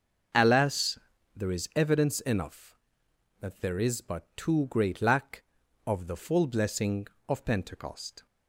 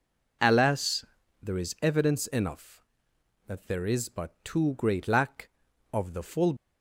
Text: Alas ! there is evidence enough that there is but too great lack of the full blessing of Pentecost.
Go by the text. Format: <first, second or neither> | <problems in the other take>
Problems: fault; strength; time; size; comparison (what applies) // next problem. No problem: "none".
first | stops before "blessing of Pentecost"; at 6.5 s